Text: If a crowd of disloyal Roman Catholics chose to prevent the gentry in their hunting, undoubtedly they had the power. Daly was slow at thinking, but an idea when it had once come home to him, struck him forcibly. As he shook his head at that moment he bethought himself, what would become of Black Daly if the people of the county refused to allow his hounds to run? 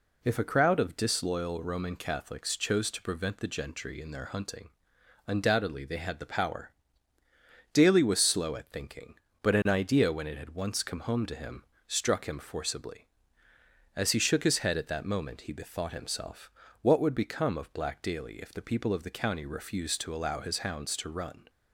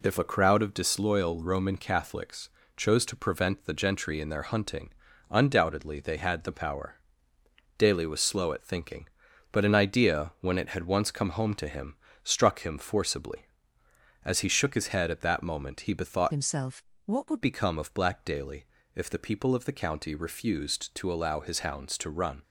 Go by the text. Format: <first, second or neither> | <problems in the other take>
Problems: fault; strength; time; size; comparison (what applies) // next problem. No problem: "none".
first | pauses between "Catholics" and "chose"; slight; at 2.4 s; 0.26 s long // changes voice from "himself" to "would"; from 16.3 to 17.4 s; 1.1 s long // pauses between "Daly" and "if"; slight; at 18.6 s; 0.30 s long